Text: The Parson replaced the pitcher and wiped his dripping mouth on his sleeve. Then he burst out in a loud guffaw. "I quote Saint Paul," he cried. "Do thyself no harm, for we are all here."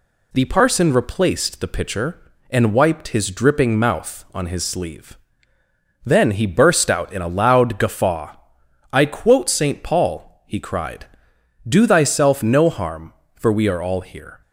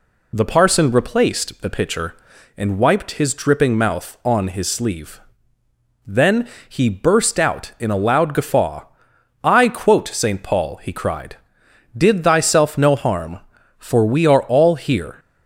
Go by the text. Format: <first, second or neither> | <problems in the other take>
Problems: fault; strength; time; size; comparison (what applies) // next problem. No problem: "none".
first | pauses between "Then" and "he"; slight; at 6.4 s; 0.20 s long // says "Did" for "Do"; at 11.9 s